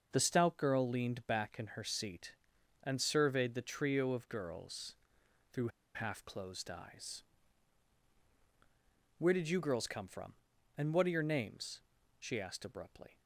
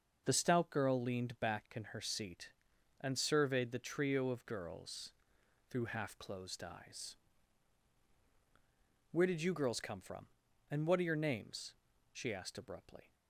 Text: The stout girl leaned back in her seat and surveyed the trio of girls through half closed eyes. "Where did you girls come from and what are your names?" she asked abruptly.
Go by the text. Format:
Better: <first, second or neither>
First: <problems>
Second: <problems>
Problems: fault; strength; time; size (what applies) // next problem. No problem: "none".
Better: second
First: starts louder than the rest; noticeable; until 1.1 s; 6 dB // pauses between "girls" and "through"; noticeable; at 4.9 s; 0.58 s long // pauses between "through" and "half"; slight; at 5.6 s; 0.26 s long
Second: starts louder than the rest; noticeable; until 1.2 s; 6 dB // pauses between "girls" and "through"; noticeable; at 5.1 s; 0.58 s long